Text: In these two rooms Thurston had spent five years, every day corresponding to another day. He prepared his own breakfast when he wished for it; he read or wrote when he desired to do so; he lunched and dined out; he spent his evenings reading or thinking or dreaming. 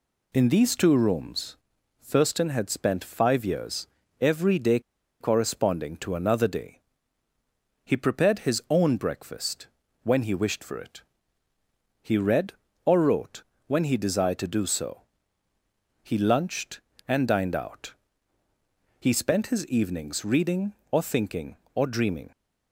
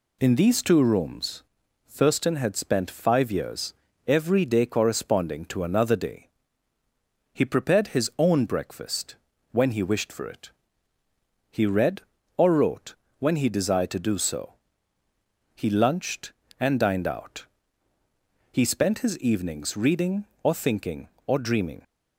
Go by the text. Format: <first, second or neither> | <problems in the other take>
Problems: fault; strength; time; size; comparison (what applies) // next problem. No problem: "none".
second | pauses between "rooms" and "Thurston"; noticeable; at 1.5 s; 0.46 s long; noticeable in the second // pauses between "day" and "corresponding"; at 4.7 s; 0.40 s long // pauses between "breakfast" and "when"; at 9.6 s; 0.38 s long; also in the second // pauses between "wrote" and "when"; slight; at 13.4 s; 0.24 s long; slight in the second